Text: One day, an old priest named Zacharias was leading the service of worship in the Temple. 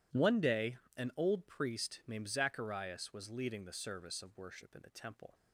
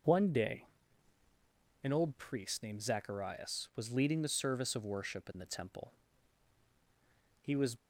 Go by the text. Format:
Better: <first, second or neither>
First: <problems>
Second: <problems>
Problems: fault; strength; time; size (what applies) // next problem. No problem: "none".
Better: first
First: none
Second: goes on to say "He was"; slight; from 7.4 s on; 0.34 s long